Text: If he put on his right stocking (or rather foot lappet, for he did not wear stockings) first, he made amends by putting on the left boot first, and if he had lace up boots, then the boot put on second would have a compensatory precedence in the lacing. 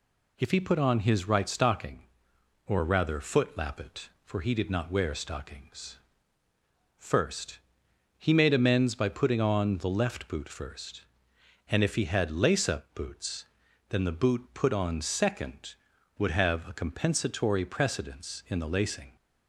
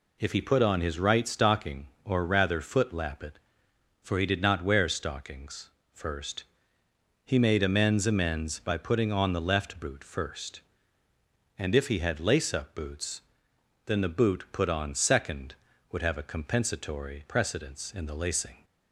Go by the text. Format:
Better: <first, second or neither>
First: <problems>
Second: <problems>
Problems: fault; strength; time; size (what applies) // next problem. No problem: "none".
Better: first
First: none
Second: says "amends" twice; at 8.0 s